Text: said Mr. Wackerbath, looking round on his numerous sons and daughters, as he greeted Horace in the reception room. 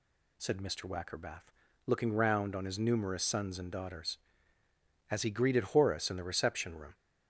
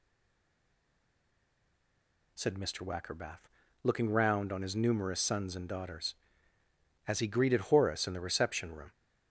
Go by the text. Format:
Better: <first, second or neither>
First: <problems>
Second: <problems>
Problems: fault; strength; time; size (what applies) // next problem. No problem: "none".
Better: first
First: none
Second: stays silent before the first word; until 2.3 s; 2.3 s long